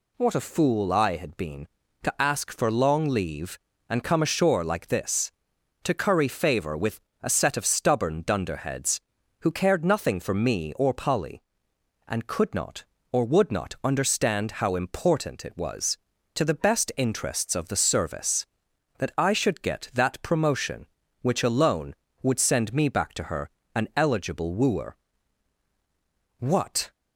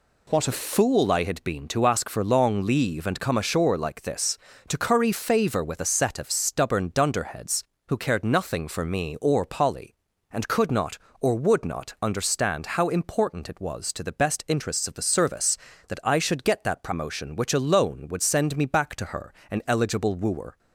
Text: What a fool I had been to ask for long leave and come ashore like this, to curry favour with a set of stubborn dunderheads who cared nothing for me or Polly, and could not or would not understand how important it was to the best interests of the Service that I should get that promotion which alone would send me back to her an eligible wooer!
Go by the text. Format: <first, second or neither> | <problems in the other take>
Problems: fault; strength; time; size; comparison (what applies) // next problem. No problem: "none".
second | pauses between "with" and "a"; slight; at 7.0 s; 0.20 s long // pauses between "her" and "an"; slight; at 23.4 s; 0.26 s long; slight in the second // goes on to say "What"; from 26.3 s on; 0.54 s long